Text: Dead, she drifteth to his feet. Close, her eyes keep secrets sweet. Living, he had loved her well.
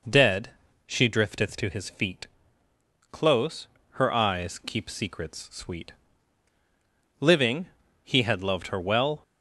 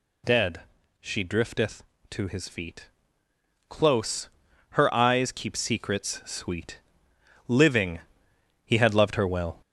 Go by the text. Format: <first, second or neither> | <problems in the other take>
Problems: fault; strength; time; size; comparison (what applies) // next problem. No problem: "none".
first | gets louder; throughout; 4 dB